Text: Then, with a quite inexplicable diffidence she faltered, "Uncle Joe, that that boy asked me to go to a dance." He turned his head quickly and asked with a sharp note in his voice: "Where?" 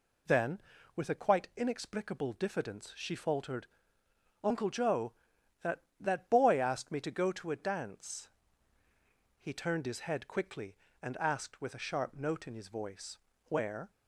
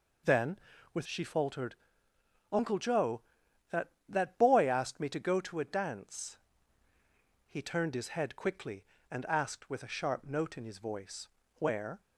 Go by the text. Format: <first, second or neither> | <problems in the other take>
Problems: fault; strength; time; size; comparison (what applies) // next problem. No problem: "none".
first | skips "a quite inexplicable diffidence"; at 1.0 s